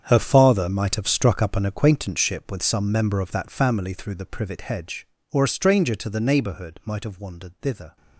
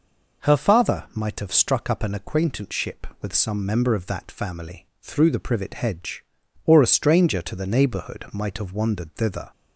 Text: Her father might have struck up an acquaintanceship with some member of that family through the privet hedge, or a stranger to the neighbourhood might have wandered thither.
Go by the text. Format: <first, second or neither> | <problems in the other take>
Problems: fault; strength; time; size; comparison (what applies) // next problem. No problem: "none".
second | gets quieter; strong; throughout; 14.5 dB